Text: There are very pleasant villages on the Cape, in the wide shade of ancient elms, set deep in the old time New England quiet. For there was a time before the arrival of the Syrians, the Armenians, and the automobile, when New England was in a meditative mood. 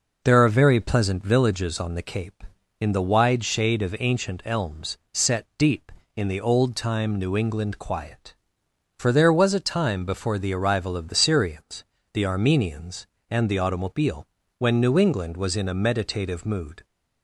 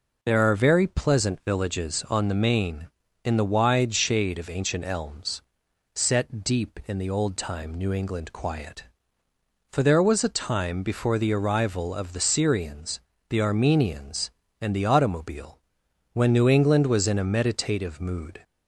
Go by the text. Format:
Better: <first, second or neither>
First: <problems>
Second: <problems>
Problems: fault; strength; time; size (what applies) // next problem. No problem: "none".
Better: first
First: none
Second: says "Main" for "Cape"; at 2.3 s